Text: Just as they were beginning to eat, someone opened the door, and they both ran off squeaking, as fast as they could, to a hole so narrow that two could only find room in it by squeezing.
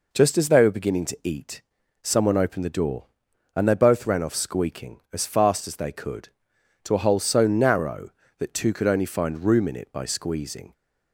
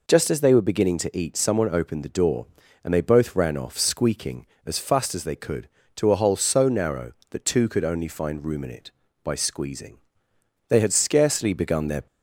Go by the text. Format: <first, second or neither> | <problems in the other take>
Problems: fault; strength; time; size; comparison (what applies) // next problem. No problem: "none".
first | goes on to say "They had scarcely begun their"; from 10.6 s on; 1.3 s long